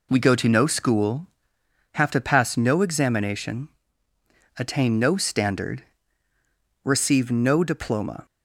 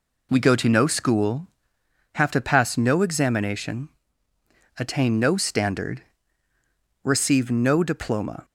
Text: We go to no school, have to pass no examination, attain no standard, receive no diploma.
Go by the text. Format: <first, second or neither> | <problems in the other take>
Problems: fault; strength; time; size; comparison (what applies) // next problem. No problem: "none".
neither | none